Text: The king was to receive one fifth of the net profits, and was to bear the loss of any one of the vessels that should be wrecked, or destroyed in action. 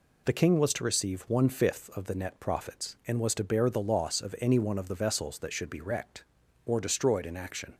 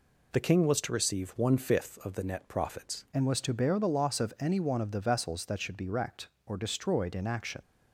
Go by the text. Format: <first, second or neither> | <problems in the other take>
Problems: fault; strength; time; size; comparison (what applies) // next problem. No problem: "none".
first | changes voice at "and"; from 3.1 s on; 4.5 s long